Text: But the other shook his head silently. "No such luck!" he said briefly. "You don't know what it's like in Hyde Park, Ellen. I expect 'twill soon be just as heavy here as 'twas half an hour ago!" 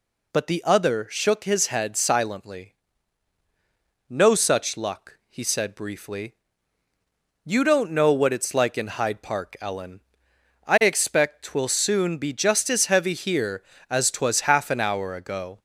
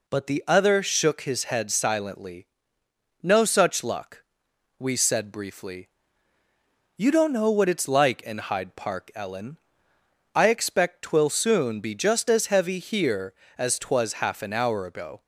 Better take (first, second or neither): first